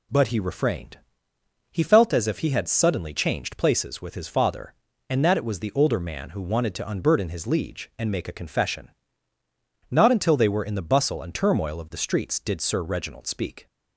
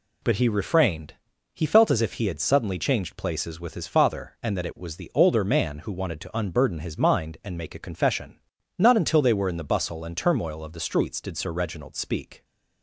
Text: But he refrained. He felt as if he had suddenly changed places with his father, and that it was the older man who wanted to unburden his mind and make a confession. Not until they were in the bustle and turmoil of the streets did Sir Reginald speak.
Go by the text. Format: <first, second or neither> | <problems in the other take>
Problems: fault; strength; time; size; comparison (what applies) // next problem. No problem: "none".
second | says "liege" for "mind"; at 7.4 s